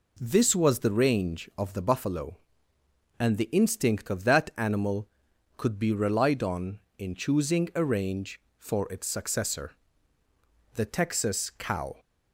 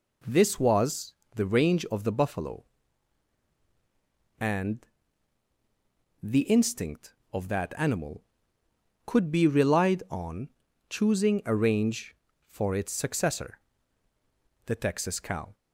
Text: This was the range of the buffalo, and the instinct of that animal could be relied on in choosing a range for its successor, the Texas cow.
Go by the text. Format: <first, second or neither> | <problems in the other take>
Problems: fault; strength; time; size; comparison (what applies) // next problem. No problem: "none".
first | pauses between "was" and "the"; slight; at 1.1 s; 0.20 s long // pauses between "and" and "the"; strong; at 4.8 s; 1.3 s long // skips "in"; at 10.6 s